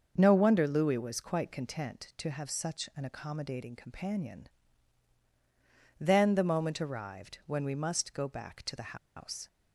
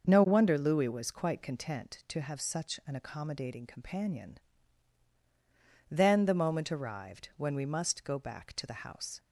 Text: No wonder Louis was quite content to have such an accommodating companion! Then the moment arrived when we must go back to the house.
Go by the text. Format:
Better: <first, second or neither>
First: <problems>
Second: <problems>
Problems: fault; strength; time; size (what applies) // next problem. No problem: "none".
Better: second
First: starts louder than the rest; until 1.1 s; 6.5 dB // pauses between "the" and "house"; slight; at 8.9 s; 0.19 s long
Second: starts louder than the rest; noticeable; until 1.1 s; 6 dB